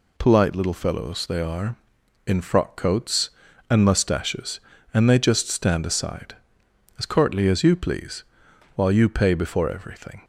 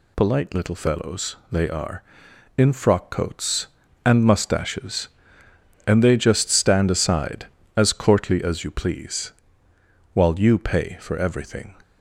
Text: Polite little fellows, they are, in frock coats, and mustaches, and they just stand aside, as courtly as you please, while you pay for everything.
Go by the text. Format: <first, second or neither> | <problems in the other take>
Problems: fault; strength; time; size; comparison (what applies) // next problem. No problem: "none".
second | says "before" for "for"; at 9.3 s